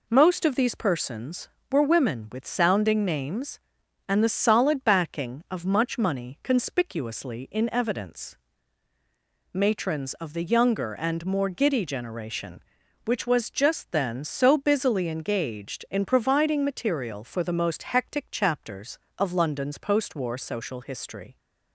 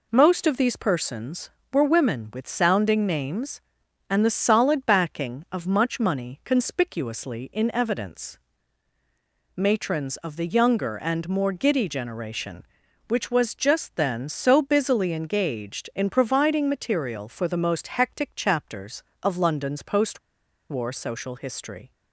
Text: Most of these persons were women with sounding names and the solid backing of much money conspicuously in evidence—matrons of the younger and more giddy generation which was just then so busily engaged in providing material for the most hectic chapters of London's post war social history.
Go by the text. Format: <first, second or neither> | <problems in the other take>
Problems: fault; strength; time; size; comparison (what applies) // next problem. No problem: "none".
first | pauses between "post" and "war"; noticeable; at 20.1 s; 0.51 s long